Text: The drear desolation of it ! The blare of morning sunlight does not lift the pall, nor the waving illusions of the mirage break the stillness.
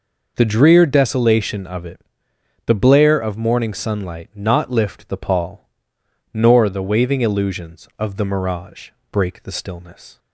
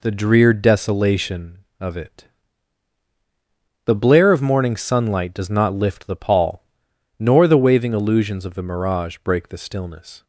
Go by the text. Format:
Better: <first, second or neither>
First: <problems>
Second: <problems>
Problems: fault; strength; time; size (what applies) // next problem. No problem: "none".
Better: second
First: skips "does"; at 4.3 s // pauses between "mirage" and "break"; slight; at 8.9 s; 0.22 s long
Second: none